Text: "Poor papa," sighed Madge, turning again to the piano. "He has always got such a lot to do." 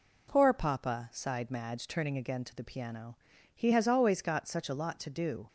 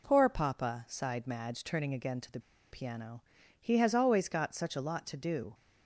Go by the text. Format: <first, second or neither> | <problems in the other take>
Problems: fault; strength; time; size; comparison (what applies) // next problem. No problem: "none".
first | pauses between "the" and "piano"; slight; at 2.3 s; 0.32 s long